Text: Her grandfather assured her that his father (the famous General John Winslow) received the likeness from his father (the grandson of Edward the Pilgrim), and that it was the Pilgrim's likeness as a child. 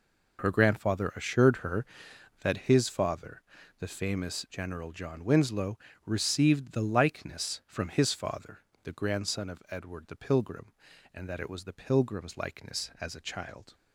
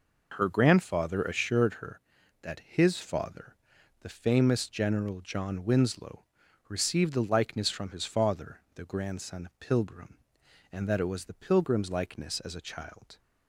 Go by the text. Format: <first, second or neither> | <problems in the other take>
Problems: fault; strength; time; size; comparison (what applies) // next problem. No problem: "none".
first | skips "of Edward the"; at 9.5 s